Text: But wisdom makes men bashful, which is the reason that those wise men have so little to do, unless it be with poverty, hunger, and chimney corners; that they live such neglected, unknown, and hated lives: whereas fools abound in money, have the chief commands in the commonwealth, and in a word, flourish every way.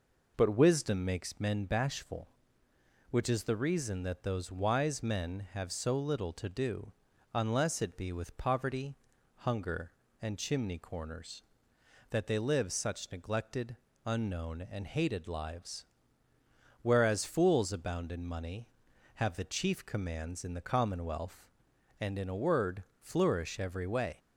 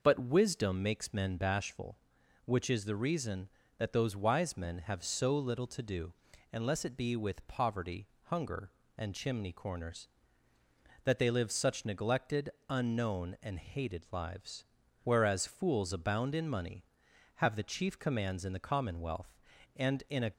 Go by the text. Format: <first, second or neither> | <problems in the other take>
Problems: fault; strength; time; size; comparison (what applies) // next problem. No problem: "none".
first | stops before "word flourish every way"; at 20.3 s